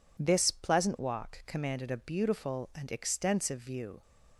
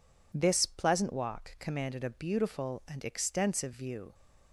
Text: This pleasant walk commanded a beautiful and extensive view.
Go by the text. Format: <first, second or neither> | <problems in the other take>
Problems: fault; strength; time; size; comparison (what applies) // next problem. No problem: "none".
neither | none